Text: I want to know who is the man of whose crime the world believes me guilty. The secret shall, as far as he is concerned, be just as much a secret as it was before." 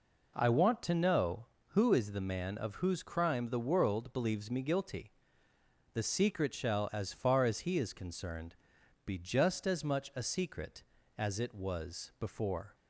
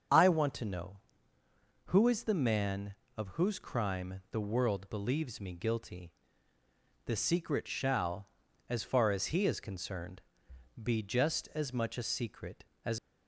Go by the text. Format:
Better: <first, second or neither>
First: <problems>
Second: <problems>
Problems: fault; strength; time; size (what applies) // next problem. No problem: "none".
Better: first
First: none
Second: starts louder than the rest; until 2.0 s; 6.5 dB // stops before "it was before"; at 12.9 s